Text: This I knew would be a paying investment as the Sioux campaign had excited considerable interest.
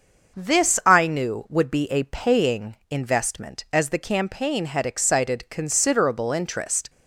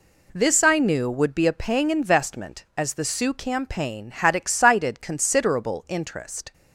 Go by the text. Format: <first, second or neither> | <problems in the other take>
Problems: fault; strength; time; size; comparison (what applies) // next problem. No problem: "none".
second | starts louder than the rest; until 1.4 s; 6 dB // skips "Sioux"; at 3.9 s